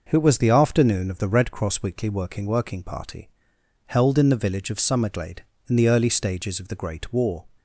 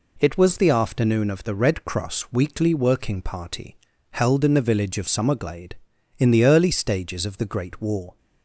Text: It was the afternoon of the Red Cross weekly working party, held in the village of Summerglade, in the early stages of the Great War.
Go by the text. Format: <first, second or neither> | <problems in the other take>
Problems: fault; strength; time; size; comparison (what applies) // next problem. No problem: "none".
second | says "working" twice; at 2.4 s